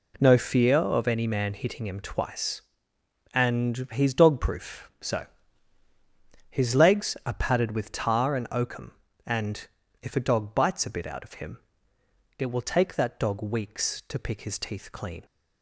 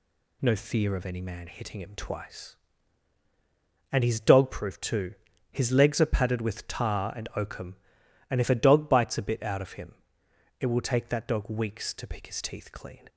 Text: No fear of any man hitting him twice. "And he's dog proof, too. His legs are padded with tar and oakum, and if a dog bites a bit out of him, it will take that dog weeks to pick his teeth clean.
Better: second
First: says "so" for "too"; at 5.0 s // pauses between "and" and "if"; slight; at 9.6 s; 0.34 s long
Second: none

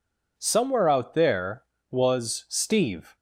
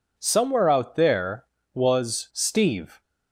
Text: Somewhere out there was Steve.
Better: neither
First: none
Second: none

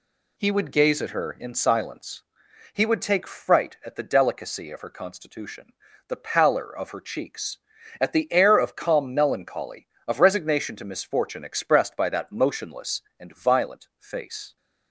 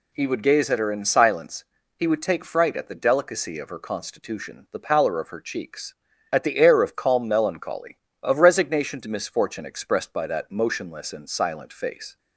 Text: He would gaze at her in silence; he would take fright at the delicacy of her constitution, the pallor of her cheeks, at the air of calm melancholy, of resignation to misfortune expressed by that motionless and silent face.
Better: second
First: says "violent" for "silent"; at 13.3 s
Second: none

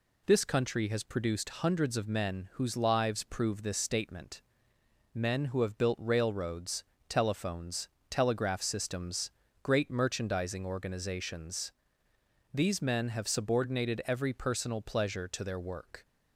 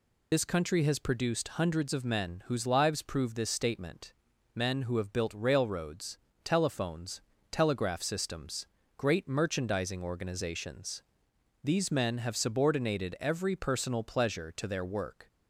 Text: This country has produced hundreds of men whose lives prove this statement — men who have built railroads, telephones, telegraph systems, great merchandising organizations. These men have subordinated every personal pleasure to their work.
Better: first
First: none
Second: loses the start of "This"; at 0.3 s; 55 ms

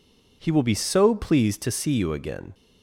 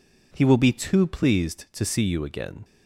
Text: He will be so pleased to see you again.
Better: first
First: none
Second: says "too" for "so"; at 0.7 s

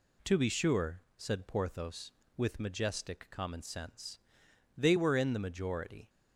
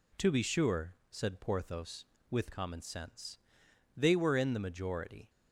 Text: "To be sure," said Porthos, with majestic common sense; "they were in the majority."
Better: first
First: none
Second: skips "majestic"; at 2.5 s

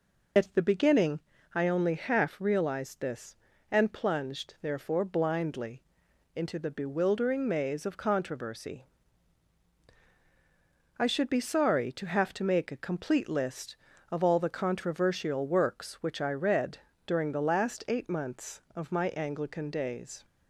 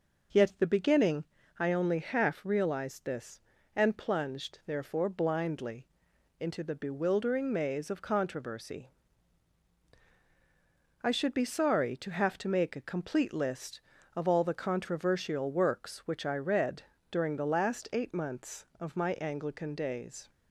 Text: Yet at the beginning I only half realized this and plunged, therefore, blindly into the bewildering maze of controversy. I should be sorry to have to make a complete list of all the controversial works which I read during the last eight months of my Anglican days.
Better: second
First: loses the start of "Yet"; at 0.3 s; 90 ms // pauses between "beginning" and "I"; slight; at 1.2 s; 0.34 s long // pauses between "blindly" and "into"; noticeable; at 5.8 s; 0.52 s long // pauses between "read" and "during"; slight; at 16.7 s; 0.28 s long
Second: pauses between "beginning" and "I"; slight; at 1.2 s; 0.34 s long // pauses between "blindly" and "into"; noticeable; at 5.8 s; 0.52 s long // pauses between "read" and "during"; slight; at 16.8 s; 0.28 s long

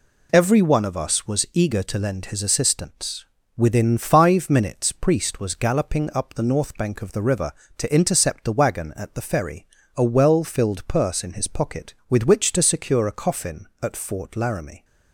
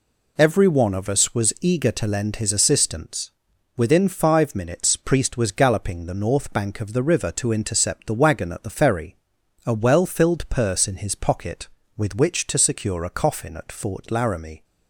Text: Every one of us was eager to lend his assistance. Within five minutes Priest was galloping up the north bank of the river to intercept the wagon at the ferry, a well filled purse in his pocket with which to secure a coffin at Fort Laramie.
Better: first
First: none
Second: skips "up"; at 6.0 s

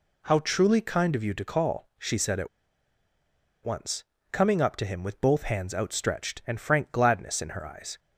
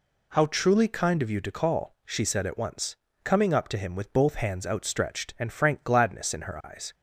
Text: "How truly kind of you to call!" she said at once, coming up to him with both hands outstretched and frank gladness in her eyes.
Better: second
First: pauses between "at" and "once"; at 2.4 s; 1.1 s long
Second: none

